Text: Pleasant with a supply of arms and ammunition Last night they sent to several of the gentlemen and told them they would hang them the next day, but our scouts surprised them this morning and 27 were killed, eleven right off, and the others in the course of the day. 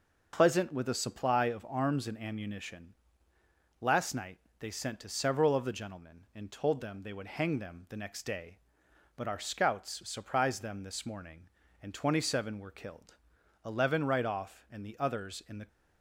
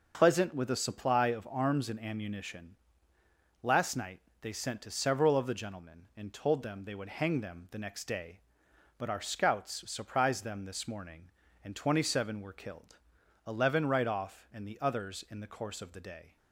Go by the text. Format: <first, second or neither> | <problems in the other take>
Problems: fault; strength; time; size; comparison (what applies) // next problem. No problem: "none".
second | starts louder than the rest; noticeable; until 1.3 s; 6 dB; noticeable in the second // pauses between "ammunition" and "Last"; noticeable; at 2.9 s; 0.86 s long; noticeable in the second // pauses between "night" and "they"; slight; at 4.3 s; 0.20 s long; slight in the second // stops before "course of the day"; at 15.6 s